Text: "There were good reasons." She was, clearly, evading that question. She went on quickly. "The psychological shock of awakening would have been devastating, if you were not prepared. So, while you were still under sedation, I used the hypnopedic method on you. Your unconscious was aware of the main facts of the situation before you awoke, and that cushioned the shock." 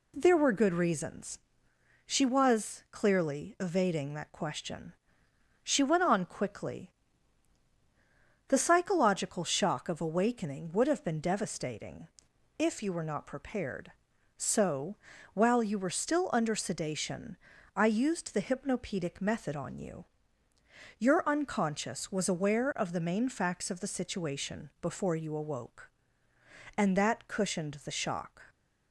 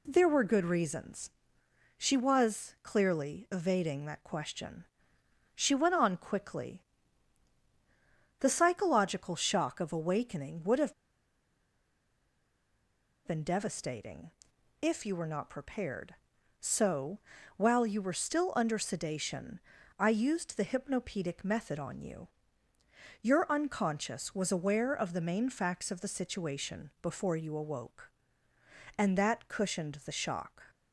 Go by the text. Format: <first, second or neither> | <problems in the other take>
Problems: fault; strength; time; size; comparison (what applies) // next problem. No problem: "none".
first | pauses between "have" and "been"; strong; at 10.9 s; 2.3 s long